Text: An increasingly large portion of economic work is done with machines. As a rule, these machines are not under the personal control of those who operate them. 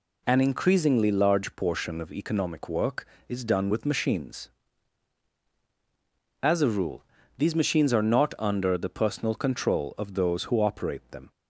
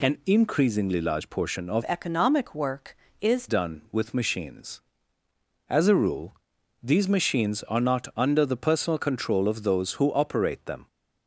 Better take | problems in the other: first | changes voice from "economic" to "is"; from 1.8 to 3.4 s; 1.6 s long

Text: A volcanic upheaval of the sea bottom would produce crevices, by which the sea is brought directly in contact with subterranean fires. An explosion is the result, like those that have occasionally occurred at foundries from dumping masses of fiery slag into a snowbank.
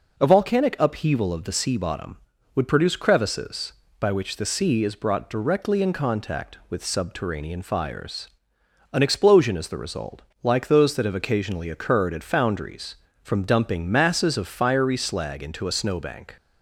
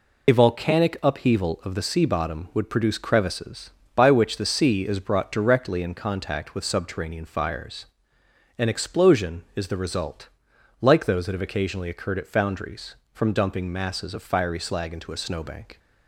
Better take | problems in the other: first | loses the start of "A"; at 0.2 s; 35 ms

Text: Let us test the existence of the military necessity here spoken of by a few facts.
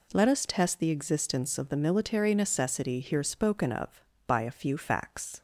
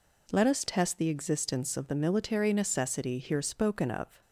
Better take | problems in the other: first | stops before "by a few facts"; at 4.2 s

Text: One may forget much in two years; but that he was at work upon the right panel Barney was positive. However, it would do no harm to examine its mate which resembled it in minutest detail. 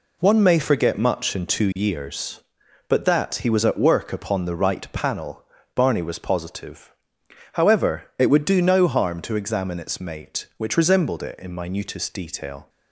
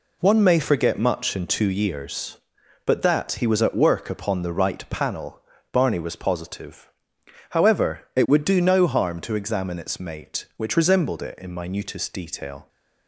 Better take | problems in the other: neither | pauses between "panel" and "Barney"; slight; the same in both

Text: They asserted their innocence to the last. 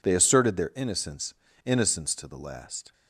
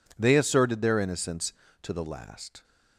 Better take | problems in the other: second | says "innocence" twice; at 1.6 s

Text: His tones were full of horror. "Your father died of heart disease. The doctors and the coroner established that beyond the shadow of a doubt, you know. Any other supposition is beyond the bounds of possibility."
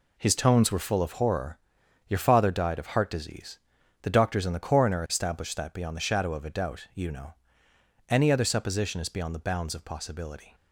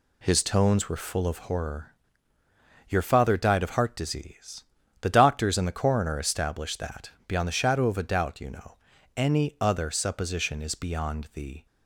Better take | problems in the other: first | pauses between "that" and "beyond"; slight; at 7.1 s; 0.16 s long // stops before "bounds of possibility"; at 11.6 s

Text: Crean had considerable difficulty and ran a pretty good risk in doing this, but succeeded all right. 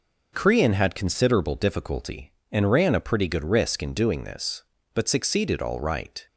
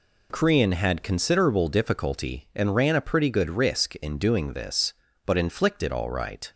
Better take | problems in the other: first | says "inflicted" for "succeeded"; at 5.3 s

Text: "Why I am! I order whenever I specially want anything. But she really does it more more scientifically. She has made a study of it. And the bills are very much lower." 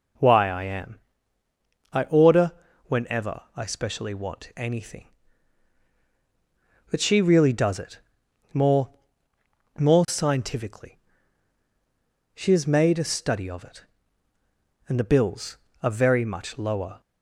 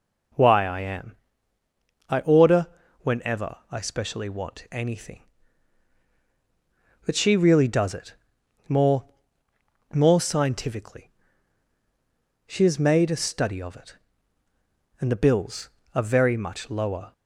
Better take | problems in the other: neither | pauses between "order" and "whenever"; slight; the same in both // pauses between "it" and "more"; noticeable; the same in both // pauses between "more" and "more"; noticeable; the same in both

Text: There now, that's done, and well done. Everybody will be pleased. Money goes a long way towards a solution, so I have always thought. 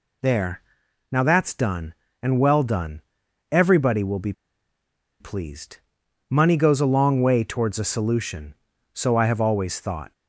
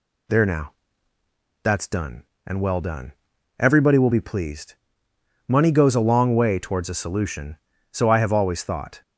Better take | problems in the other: second | pauses between "There" and "now"; noticeable; at 0.6 s; 0.50 s long // pauses between "be" and "pleased"; noticeable; at 4.3 s; 0.88 s long

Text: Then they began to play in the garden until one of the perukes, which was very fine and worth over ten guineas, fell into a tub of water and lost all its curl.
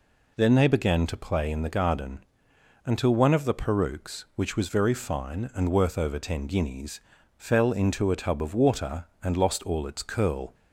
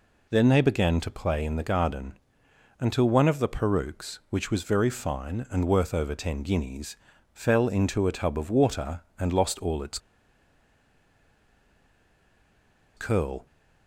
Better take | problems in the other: first | pauses between "garden" and "until"; noticeable; at 2.1 s; 0.60 s long; noticeable in the first // pauses between "its" and "curl"; strong; at 9.9 s; 2.9 s long

